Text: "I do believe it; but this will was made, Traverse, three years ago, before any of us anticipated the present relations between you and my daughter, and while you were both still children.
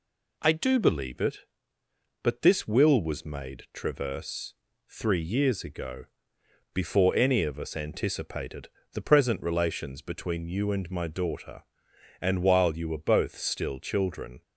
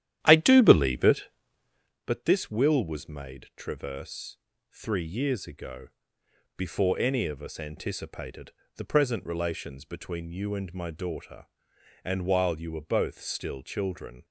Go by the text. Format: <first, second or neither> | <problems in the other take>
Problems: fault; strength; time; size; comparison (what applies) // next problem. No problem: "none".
first | starts louder than the rest; strong; until 2.0 s; 11.5 dB // pauses between "anticipated" and "the"; slight; at 8.5 s; 0.24 s long; slight in the first